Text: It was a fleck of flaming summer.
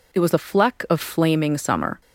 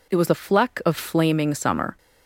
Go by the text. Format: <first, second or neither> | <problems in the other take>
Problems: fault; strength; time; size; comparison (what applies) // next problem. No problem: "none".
neither | none